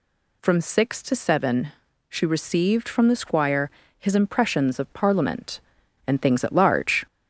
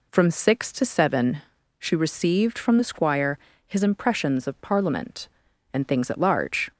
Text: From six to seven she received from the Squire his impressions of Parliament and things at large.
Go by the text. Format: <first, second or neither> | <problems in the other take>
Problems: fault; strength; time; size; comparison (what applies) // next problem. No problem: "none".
second | gets louder; slight; throughout; 2.5 dB // pauses between "seven" and "she"; at 1.7 s; 0.38 s long; also in the second // pauses between "Squire" and "his"; slight; at 3.6 s; 0.30 s long; slight in the second